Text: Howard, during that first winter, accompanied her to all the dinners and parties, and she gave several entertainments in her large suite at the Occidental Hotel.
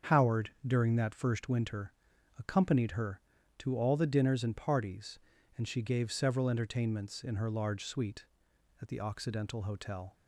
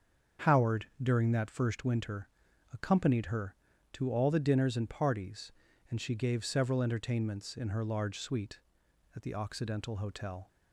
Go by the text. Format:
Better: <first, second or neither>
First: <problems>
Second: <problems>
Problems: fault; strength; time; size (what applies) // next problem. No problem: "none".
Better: neither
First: starts louder than the rest; until 1.2 s; 7 dB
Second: starts louder than the rest; until 1.5 s; 7 dB